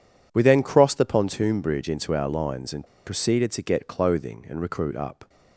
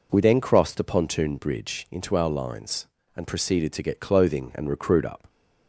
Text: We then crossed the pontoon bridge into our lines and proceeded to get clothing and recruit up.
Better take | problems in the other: second | pauses between "and" and "proceeded"; slight; at 2.8 s; 0.20 s long

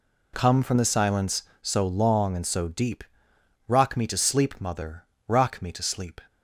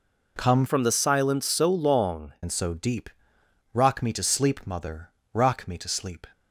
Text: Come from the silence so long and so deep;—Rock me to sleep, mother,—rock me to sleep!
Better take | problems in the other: first | changes voice from "from" to "long"; from 0.6 to 2.3 s; 1.7 s long

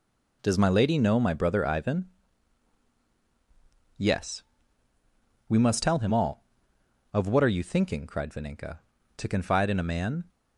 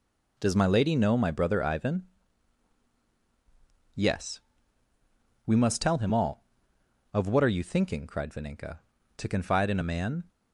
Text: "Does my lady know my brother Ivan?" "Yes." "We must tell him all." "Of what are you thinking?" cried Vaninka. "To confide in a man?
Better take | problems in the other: neither | none

